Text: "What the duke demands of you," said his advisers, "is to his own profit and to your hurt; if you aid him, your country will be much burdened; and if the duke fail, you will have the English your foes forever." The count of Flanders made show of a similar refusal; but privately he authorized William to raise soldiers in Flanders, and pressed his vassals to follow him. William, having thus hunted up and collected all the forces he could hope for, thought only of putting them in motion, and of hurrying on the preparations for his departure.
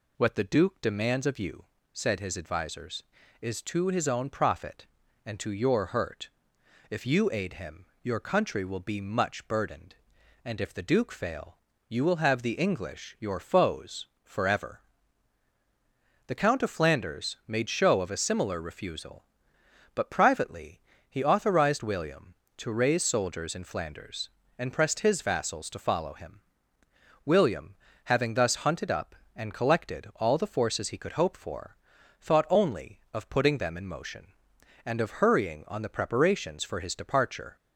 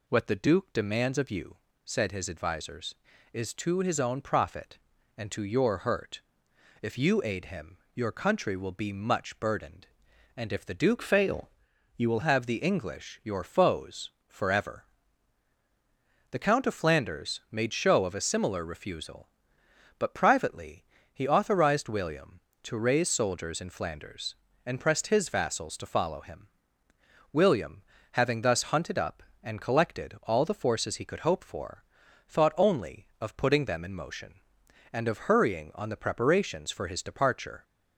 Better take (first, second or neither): first